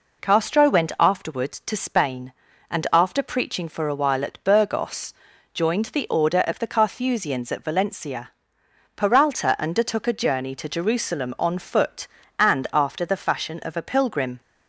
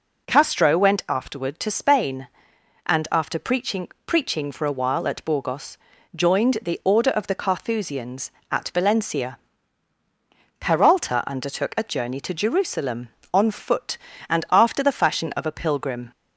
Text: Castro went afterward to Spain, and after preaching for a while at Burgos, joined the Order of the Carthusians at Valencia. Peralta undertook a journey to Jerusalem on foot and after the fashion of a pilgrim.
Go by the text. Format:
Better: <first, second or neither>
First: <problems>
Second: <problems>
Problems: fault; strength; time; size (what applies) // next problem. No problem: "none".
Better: first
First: none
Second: says "preaching" twice; at 4.0 s